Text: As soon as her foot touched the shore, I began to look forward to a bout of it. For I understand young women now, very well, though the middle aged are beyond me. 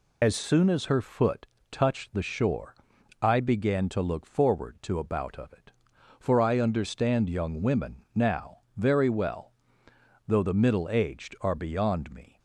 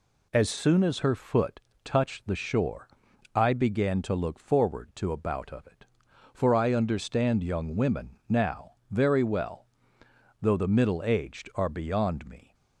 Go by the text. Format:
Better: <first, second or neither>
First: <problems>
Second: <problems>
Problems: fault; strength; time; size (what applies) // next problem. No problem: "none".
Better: second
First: loses the start of "As"; at 0.2 s; 55 ms // pauses between "foot" and "touched"; slight; at 1.4 s; 0.28 s long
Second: pauses between "foot" and "touched"; slight; at 1.5 s; 0.27 s long